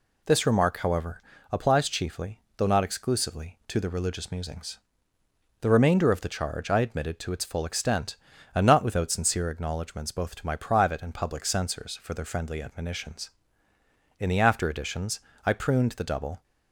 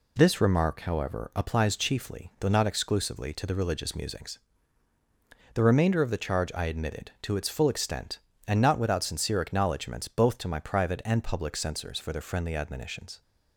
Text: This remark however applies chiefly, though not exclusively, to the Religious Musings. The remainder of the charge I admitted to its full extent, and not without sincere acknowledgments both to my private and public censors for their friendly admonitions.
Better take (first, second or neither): second